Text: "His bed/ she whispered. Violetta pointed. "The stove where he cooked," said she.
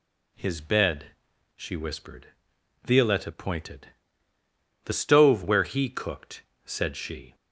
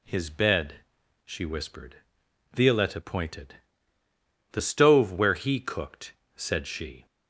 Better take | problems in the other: neither | none

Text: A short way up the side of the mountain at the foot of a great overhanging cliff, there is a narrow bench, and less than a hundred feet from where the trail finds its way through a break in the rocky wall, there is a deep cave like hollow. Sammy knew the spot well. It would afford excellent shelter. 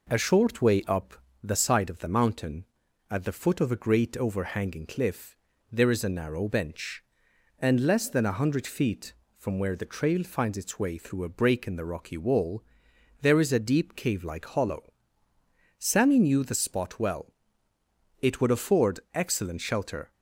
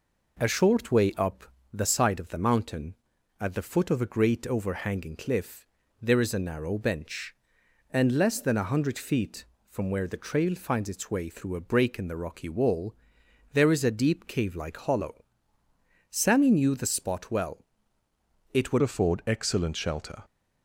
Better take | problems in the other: first | pauses between "up" and "the"; slight; at 1.4 s; 0.28 s long; slight in the first // changes voice at "afford"; from 18.8 s on; 1.4 s long

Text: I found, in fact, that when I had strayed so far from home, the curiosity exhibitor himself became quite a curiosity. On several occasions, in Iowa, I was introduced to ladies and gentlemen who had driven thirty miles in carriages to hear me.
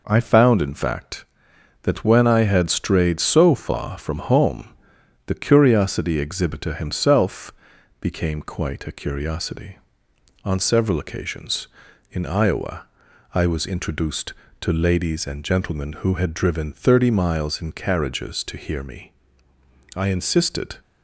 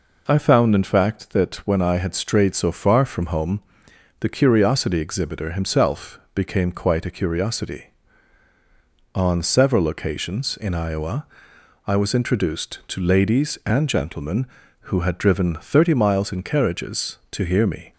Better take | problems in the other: second | pauses between "himself" and "became"; noticeable; at 7.5 s; 0.48 s long; slight in the second // goes on to say "I insisted"; noticeable; from 19.9 s on; 0.82 s long

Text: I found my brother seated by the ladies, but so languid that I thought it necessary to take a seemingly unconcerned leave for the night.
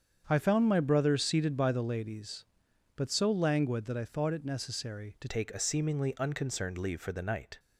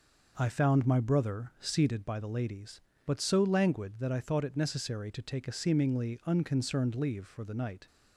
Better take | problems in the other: second | starts louder than the rest; strong; until 1.2 s; 7.5 dB // changes voice at "take"; from 5.2 s on; 2.3 s long

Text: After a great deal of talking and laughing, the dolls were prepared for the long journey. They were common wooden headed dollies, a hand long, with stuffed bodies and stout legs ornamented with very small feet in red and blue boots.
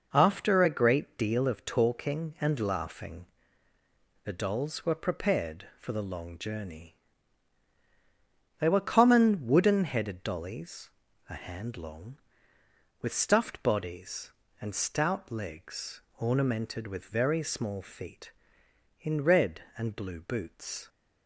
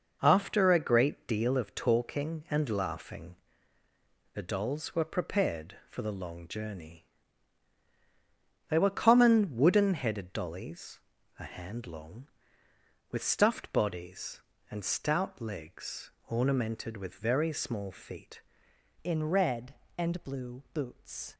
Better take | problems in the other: first | pauses between "legs" and "ornamented"; slight; at 16.1 s; 0.16 s long; slight in the first // changes voice at "in"; from 19.0 s on; 2.3 s long

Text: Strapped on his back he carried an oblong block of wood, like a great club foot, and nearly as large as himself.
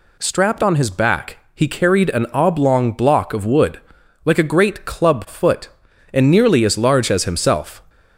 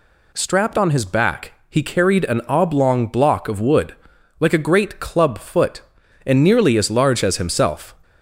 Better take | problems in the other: neither | pauses between "back" and "he"; slight; the same in both

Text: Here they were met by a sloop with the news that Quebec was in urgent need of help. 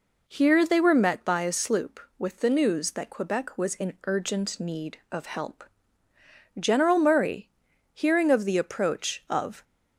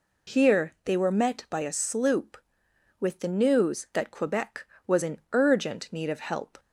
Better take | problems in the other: second | goes on to say "General Murray hearing of the approach of"; strong; from 6.5 s on; 3.0 s long

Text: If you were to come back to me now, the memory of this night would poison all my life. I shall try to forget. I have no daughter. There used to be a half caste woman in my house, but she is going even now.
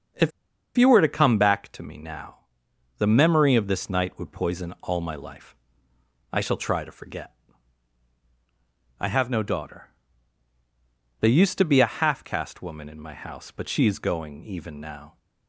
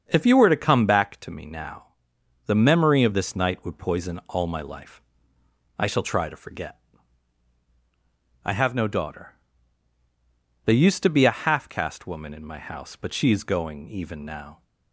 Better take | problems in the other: second | starts louder than the rest; until 1.6 s; 7 dB; also in the second // pauses between "If" and "you"; at 0.3 s; 0.45 s long

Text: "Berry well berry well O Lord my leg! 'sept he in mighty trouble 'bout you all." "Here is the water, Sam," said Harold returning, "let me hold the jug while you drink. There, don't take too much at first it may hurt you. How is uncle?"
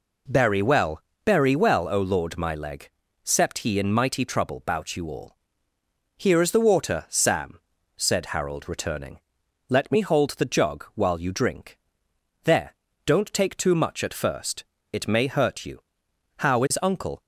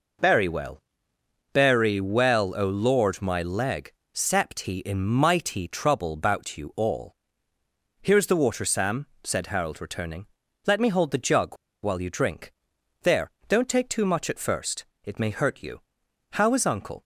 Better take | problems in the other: first | pauses between "well" and "berry"; noticeable; at 0.8 s; 0.72 s long; slight in the first // pauses between "jug" and "while"; slight; at 11.5 s; 0.27 s long // pauses between "first" and "it"; slight; at 14.8 s; 0.18 s long; slight in the first

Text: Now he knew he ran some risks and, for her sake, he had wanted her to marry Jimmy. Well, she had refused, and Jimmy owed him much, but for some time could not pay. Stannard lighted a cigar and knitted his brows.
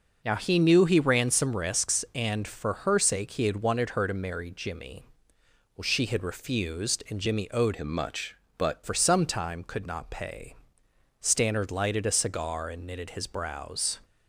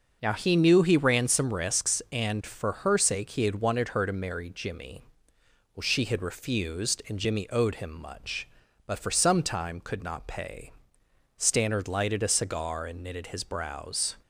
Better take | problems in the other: second | changes voice from "him" to "but"; from 7.7 to 8.8 s; 1.1 s long

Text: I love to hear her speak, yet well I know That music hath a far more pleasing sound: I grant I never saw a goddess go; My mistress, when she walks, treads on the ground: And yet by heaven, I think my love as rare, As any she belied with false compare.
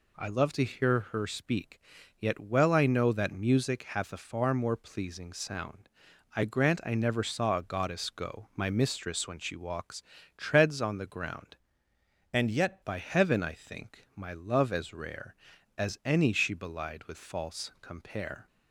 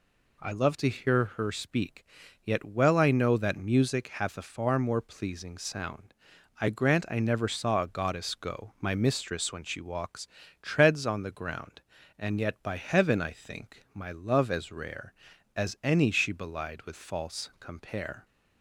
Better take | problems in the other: second | changes voice from "And" to "yet"; from 12.3 to 12.8 s; 0.5 s long

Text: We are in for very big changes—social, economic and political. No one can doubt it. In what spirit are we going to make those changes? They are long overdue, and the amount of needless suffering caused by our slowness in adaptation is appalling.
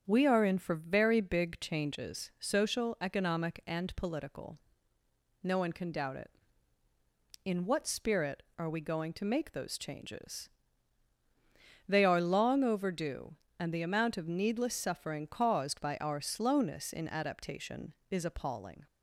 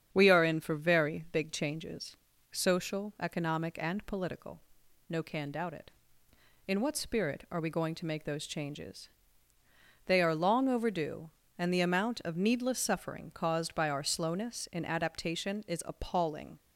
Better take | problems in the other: first | starts louder than the rest; strong; until 1.1 s; 8 dB; strong in the first // skips "one"; at 5.2 s

